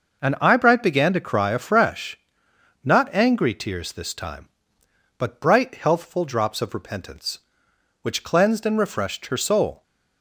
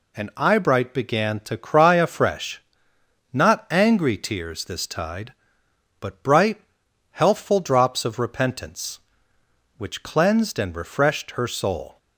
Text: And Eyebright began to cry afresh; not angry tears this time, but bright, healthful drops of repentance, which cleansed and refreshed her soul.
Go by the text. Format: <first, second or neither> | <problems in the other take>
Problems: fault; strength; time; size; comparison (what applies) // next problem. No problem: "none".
first | says "tide" for "time"; at 4.8 s